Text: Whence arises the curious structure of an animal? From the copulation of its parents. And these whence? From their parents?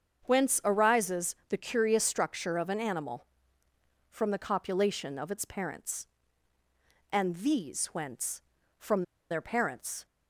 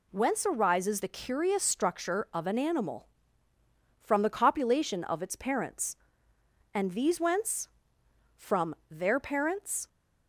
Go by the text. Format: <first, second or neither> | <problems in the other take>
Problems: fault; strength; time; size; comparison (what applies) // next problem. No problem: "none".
second | starts louder than the rest; until 1.2 s; 7 dB // pauses between "From" and "their"; slight; at 9.0 s; 0.27 s long